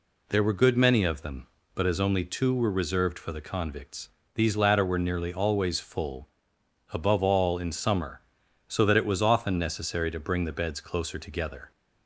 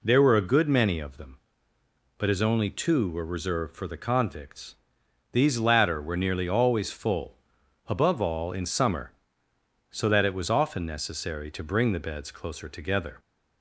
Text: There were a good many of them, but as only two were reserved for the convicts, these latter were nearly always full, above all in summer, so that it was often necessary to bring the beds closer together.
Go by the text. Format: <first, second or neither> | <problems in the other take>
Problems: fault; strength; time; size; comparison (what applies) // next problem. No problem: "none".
second | skips "a"; at 0.5 s